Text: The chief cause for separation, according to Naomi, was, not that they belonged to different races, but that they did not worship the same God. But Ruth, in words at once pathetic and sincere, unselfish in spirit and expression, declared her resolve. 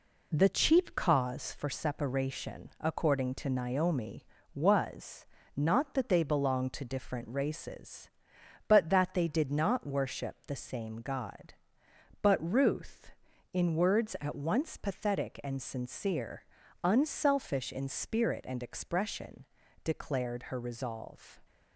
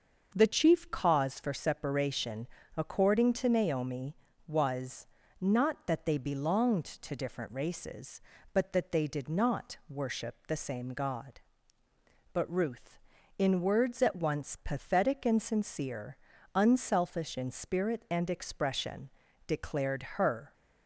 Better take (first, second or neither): first